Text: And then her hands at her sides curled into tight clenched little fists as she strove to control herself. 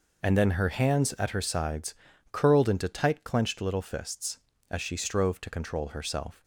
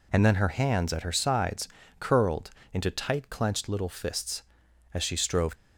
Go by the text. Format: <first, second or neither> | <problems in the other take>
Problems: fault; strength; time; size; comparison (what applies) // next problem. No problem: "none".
first | pauses between "sides" and "curled"; slight; at 1.6 s; 0.32 s long; slight in the first // pauses between "curled" and "into"; slight; at 2.4 s; 0.22 s long // stops before "to control herself"; at 5.5 s